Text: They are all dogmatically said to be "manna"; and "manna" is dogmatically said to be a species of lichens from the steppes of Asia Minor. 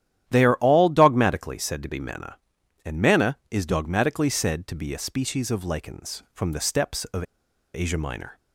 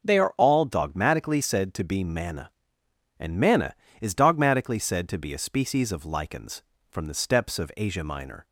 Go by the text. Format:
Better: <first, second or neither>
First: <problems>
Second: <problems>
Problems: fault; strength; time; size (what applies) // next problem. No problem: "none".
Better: second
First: starts louder than the rest; strong; until 1.2 s; 11.5 dB // pauses between "of" and "Asia"; noticeable; at 7.2 s; 0.51 s long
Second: none